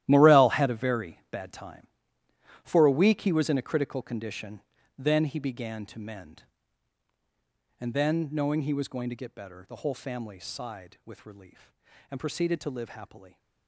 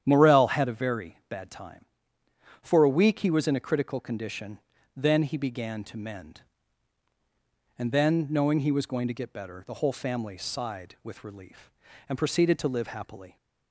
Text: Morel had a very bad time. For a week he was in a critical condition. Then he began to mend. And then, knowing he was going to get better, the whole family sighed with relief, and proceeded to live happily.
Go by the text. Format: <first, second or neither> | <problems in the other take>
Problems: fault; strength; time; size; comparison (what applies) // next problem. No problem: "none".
second | gets quieter; strong; throughout; 13.5 dB // starts louder than the rest; strong; until 1.0 s; 13 dB; strong in the second